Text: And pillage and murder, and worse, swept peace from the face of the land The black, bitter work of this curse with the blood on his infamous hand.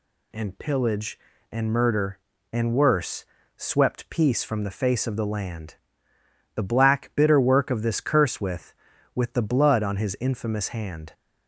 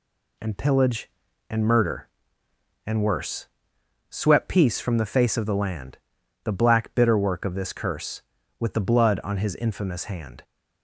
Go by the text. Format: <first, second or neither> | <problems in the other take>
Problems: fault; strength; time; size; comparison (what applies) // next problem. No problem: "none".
second | pauses between "land" and "The"; noticeable; at 5.7 s; 0.78 s long; noticeable in the second // says "with" twice; at 9.1 s